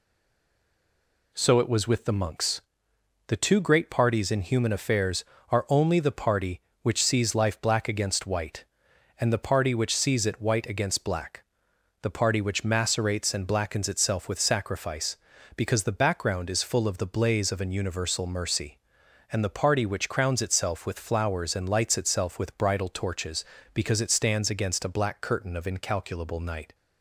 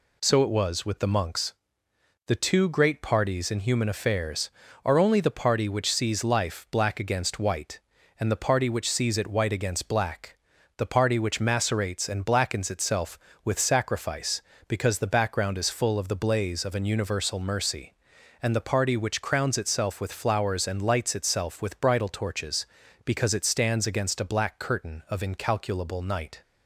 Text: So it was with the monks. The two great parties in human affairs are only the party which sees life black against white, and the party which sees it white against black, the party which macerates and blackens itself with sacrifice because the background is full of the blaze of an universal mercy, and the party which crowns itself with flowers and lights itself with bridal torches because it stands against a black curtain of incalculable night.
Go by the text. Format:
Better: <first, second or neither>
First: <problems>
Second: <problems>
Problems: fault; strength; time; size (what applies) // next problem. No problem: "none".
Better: second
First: stays silent before the first word; noticeable; until 1.3 s; 1.3 s long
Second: none